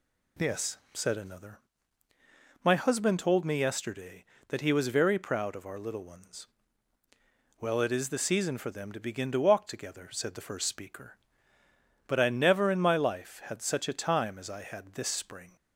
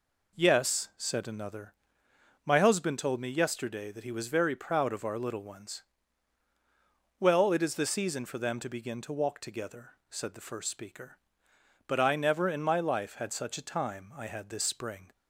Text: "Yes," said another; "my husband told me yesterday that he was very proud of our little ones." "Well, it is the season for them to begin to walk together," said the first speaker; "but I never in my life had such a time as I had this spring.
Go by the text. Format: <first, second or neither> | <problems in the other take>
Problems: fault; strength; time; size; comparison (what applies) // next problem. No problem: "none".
first | skips "as"; at 14.1 s